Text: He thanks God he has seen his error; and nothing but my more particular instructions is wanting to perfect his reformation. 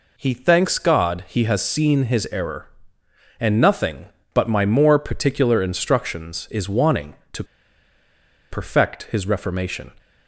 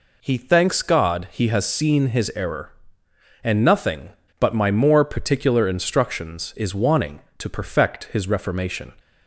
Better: second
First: pauses between "to" and "perfect"; at 7.4 s; 1.0 s long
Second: none

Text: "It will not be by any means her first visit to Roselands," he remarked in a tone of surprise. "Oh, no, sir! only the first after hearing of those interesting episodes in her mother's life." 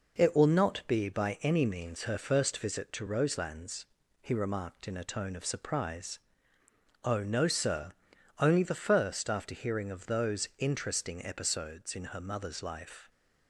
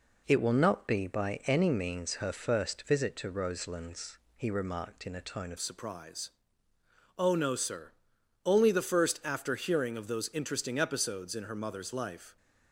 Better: first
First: none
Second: changes voice at "surprise"; from 5.5 s on; 6.8 s long

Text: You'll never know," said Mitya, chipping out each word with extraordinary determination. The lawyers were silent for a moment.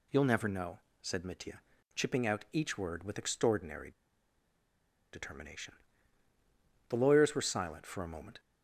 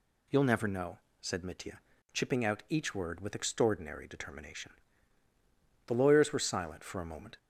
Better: second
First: pauses between "extraordinary" and "determination"; at 3.9 s; 1.2 s long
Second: none

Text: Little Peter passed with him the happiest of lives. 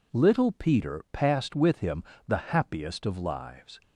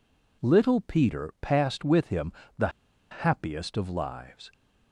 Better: first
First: pauses between "him" and "the"; slight; at 2.0 s; 0.24 s long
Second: pauses between "him" and "the"; slight; at 2.3 s; 0.26 s long // pauses between "the" and "happiest"; at 2.6 s; 0.42 s long

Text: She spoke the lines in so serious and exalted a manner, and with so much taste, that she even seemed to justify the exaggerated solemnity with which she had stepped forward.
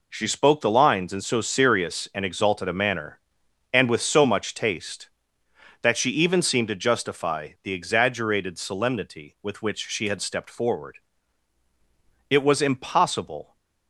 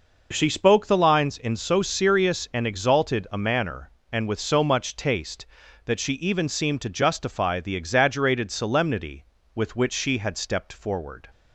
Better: second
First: goes on to say "It was impossible"; noticeable; from 12.2 s on; 1.2 s long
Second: none

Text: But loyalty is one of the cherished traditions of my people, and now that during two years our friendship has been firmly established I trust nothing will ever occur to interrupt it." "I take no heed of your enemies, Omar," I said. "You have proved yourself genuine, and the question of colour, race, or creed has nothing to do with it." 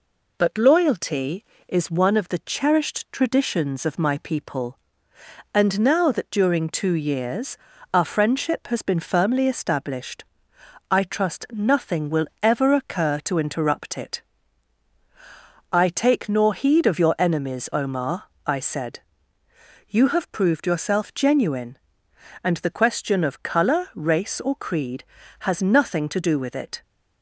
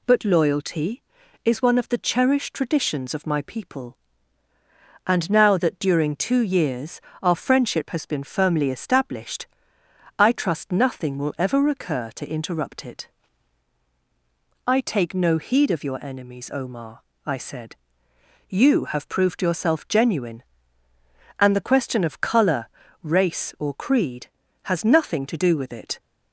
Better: second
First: pauses between "years" and "our"; slight; at 7.5 s; 0.36 s long // pauses between "established" and "I"; noticeable; at 10.2 s; 0.66 s long // pauses between "will" and "ever"; slight; at 12.2 s; 0.16 s long // says "nor" for "no"; at 16.2 s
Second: pauses between "years" and "our"; slight; at 6.9 s; 0.22 s long // pauses between "established" and "I"; noticeable; at 9.4 s; 0.72 s long

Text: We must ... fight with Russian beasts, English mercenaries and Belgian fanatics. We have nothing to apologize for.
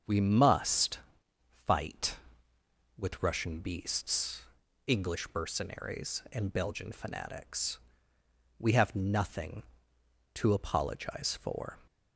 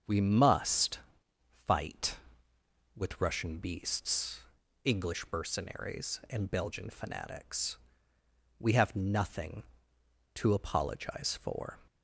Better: neither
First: starts louder than the rest; strong; until 1.7 s; 7.5 dB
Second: starts louder than the rest; strong; until 1.7 s; 7.5 dB

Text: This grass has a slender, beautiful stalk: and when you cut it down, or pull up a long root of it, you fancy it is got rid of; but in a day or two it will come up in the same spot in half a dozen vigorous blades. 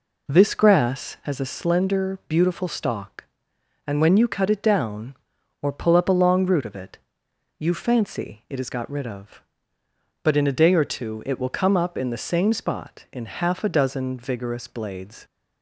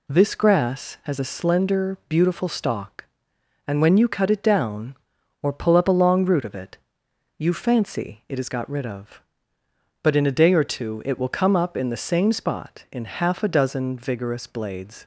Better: second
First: starts louder than the rest; until 1.5 s; 4 dB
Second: none

